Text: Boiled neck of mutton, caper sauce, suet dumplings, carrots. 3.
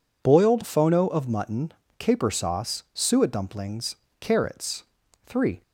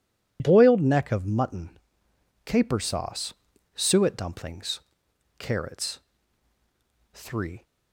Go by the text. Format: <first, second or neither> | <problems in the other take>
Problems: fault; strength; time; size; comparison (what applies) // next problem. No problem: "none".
second | says "phono" for "neck"; at 0.6 s